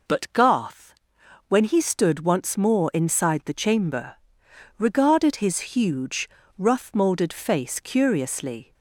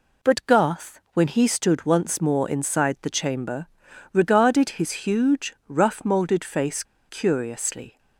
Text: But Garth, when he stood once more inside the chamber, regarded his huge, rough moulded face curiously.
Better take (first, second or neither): first